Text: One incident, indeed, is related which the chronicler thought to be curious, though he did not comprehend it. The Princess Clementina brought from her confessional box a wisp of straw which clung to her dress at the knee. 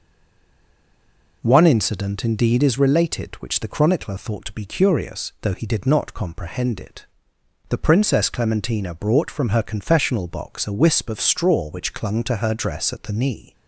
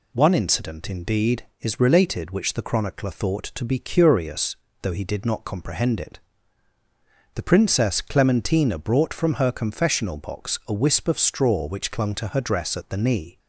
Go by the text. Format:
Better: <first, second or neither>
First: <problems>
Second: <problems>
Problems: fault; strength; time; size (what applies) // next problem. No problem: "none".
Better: second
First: stays silent before the first word; noticeable; until 1.4 s; 1.4 s long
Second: none